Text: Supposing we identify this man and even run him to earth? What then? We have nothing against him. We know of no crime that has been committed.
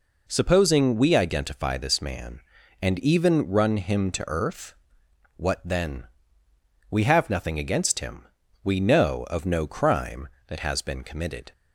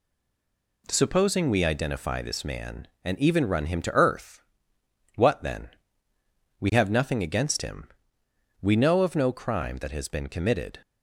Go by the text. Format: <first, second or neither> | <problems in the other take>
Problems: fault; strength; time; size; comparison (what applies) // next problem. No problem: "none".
first | stays silent before the first word; slight; until 0.8 s; 0.8 s long